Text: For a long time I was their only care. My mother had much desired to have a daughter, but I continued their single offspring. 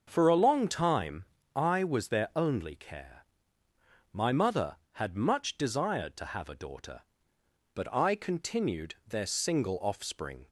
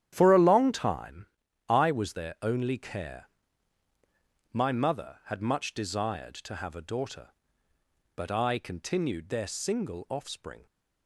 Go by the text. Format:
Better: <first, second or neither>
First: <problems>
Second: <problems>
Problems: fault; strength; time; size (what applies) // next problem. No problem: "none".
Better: first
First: starts louder than the rest; until 1.0 s; 6.5 dB // pauses between "time" and "I"; slight; at 1.2 s; 0.30 s long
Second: gets quieter; strong; throughout; 11 dB // starts louder than the rest; strong; until 1.1 s; 10.5 dB // pauses between "time" and "I"; at 1.2 s; 0.42 s long